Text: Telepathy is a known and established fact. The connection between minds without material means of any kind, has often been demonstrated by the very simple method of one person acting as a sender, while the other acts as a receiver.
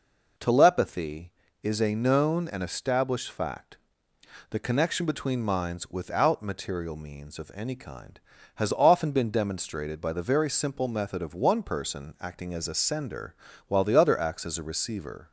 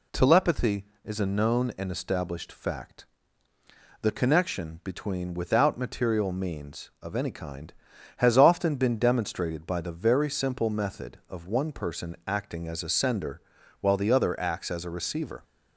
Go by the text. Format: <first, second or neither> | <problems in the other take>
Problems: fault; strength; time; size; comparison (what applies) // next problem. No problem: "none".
first | skips "minds"; at 5.3 s